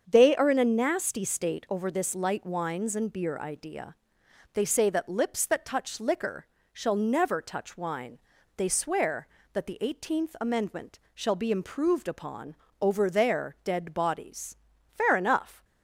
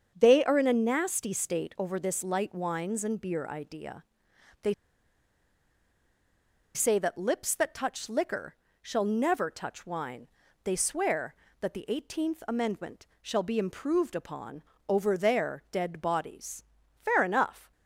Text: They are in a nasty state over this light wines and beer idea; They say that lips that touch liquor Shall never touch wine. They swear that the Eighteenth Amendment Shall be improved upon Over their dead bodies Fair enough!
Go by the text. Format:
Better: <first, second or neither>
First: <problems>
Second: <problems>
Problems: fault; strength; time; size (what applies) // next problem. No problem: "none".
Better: first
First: starts louder than the rest; until 1.0 s; 7 dB // pauses between "liquor" and "Shall"; slight; at 6.4 s; 0.28 s long // pauses between "Amendment" and "Shall"; slight; at 10.9 s; 0.16 s long // pauses between "upon" and "Over"; slight; at 12.5 s; 0.28 s long // pauses between "bodies" and "Fair"; slight; at 14.5 s; 0.36 s long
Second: starts louder than the rest; until 1.1 s; 7 dB // pauses between "They" and "say"; strong; at 4.7 s; 2.0 s long // pauses between "liquor" and "Shall"; slight; at 8.5 s; 0.28 s long // pauses between "Amendment" and "Shall"; slight; at 13.0 s; 0.16 s long // pauses between "upon" and "Over"; slight; at 14.6 s; 0.28 s long // pauses between "bodies" and "Fair"; slight; at 16.6 s; 0.36 s long